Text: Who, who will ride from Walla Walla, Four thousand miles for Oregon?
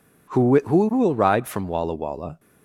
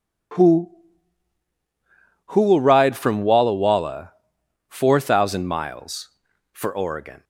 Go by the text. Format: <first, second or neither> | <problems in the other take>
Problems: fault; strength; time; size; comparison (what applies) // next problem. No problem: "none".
second | stops before "Four thousand miles for Oregon"; at 2.3 s